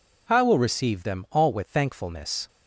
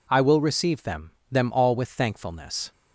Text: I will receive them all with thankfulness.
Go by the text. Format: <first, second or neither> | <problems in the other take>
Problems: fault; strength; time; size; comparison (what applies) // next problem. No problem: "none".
first | says "them" twice; at 1.3 s